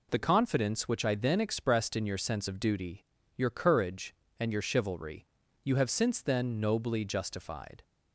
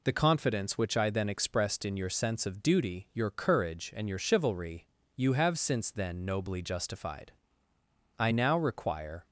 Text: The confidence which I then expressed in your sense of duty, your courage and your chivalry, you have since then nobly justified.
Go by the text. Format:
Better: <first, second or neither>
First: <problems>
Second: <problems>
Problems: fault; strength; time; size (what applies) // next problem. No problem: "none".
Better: first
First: none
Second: goes on to say "I now require"; noticeable; from 8.1 s on; 1.1 s long